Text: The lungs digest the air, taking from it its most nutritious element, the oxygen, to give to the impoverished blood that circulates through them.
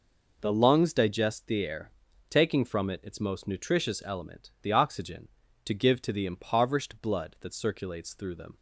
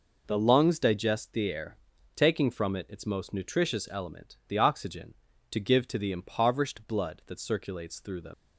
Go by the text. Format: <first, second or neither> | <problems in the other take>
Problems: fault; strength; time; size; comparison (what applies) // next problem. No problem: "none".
first | leaves "them" unfinished; at 8.3 s; 80 ms